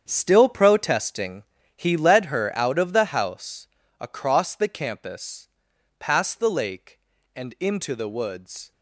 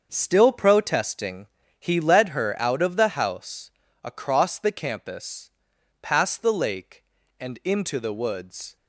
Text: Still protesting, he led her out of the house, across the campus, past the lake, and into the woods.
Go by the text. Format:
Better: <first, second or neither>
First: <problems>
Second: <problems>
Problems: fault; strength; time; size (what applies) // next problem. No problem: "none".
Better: second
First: gets quieter; strong; throughout; 12 dB // starts louder than the rest; strong; until 1.0 s; 8 dB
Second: starts louder than the rest; until 1.1 s; 6.5 dB